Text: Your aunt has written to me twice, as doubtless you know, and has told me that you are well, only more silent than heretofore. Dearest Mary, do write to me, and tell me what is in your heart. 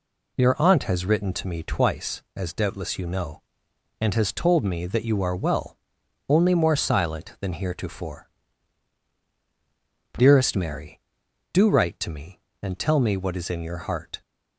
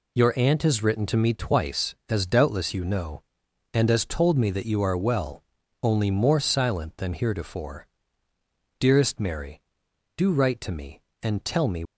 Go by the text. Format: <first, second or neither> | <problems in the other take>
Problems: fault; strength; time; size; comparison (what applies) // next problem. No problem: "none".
first | stops before "what is in your heart"; at 11.8 s